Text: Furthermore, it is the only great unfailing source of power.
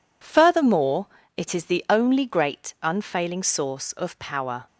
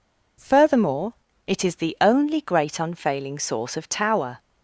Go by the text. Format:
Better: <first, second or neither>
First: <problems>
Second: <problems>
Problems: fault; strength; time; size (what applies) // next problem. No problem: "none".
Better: first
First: none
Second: says "tower" for "power"; at 3.8 s